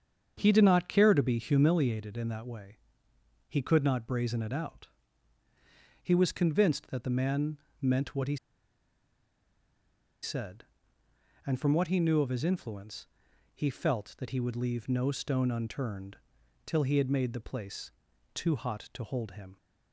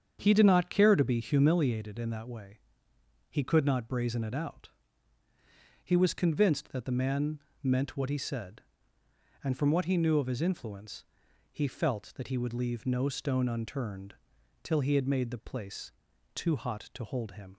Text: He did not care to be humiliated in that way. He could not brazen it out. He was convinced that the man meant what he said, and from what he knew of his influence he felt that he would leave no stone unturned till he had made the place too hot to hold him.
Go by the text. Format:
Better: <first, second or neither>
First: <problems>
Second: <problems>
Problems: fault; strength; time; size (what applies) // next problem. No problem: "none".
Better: second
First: starts louder than the rest; strong; until 1.4 s; 7.5 dB // pauses between "man" and "meant"; slight; at 7.5 s; 0.22 s long // pauses between "he" and "said"; strong; at 8.3 s; 1.8 s long // pauses between "influence" and "he"; at 13.0 s; 0.44 s long // pauses between "unturned" and "till"; noticeable; at 16.1 s; 0.48 s long // pauses between "place" and "too"; at 17.9 s; 0.44 s long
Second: starts louder than the rest; strong; until 1.2 s; 7.5 dB // pauses between "man" and "meant"; slight; at 7.3 s; 0.22 s long // pauses between "influence" and "he"; at 11.0 s; 0.44 s long // pauses between "unturned" and "till"; noticeable; at 14.1 s; 0.48 s long // pauses between "place" and "too"; at 15.9 s; 0.44 s long